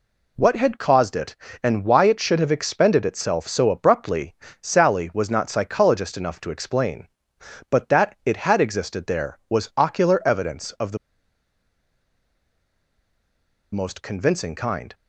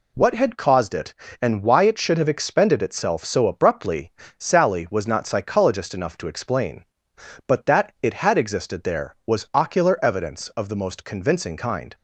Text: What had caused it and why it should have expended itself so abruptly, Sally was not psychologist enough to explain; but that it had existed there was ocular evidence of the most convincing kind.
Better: second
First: pauses between "the" and "most"; strong; at 10.9 s; 2.7 s long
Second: none

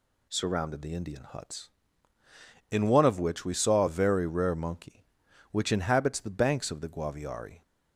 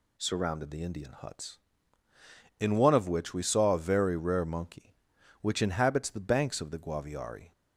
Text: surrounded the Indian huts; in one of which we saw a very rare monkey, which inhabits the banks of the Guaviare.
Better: neither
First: none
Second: none

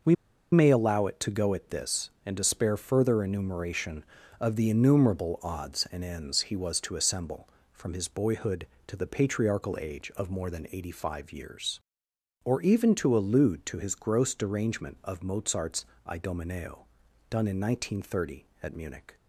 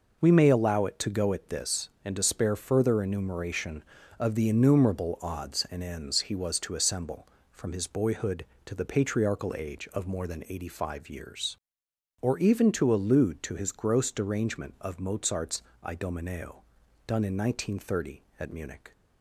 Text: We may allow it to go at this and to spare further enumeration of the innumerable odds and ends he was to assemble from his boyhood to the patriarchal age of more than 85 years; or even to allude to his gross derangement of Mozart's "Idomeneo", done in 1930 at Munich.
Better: second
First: pauses between "We" and "may"; at 0.1 s; 0.39 s long // pauses between "Mozart's" and "Idomeneo"; slight; at 15.8 s; 0.24 s long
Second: pauses between "Mozart's" and "Idomeneo"; slight; at 15.6 s; 0.24 s long

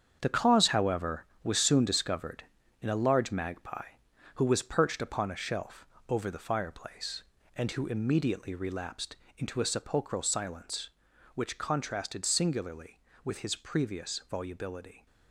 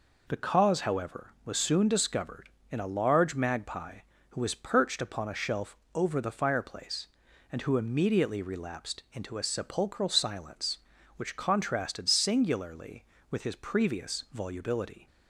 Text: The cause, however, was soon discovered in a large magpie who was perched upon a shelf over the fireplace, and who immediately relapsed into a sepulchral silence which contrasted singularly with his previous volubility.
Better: second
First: gets quieter; strong; throughout; 10 dB // pauses between "shelf" and "over"; slight; at 5.8 s; 0.22 s long // pauses between "relapsed" and "into"; slight; at 9.1 s; 0.20 s long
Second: pauses between "shelf" and "over"; slight; at 5.7 s; 0.18 s long

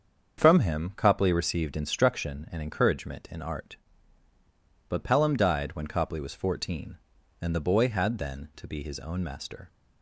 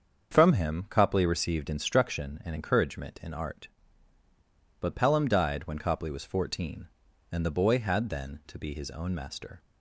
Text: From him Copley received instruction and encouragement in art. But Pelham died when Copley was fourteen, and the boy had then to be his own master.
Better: neither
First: starts louder than the rest; until 1.4 s; 7 dB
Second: starts louder than the rest; until 1.3 s; 7 dB

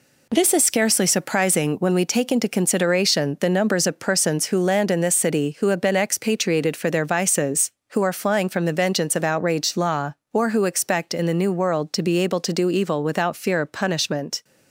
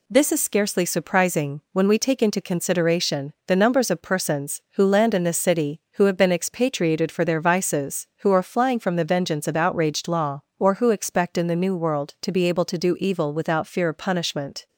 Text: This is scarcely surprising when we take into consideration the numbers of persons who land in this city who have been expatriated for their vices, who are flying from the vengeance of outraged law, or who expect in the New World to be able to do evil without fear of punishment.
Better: neither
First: none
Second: none

